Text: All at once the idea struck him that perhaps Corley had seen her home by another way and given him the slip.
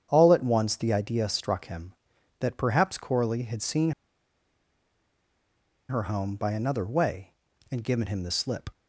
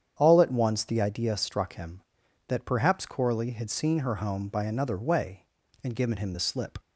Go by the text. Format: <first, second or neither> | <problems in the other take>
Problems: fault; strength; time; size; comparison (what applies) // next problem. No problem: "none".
second | starts louder than the rest; strong; until 1.1 s; 8.5 dB; strong in the second // pauses between "seen" and "her"; strong; at 3.9 s; 1.9 s long